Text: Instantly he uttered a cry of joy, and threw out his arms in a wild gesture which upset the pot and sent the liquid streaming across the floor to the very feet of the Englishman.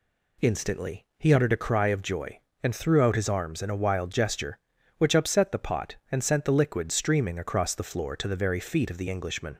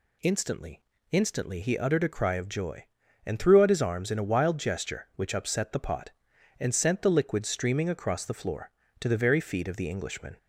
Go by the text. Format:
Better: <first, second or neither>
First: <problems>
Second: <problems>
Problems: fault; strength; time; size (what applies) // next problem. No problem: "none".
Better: first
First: none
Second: says "Instantly" twice; at 1.1 s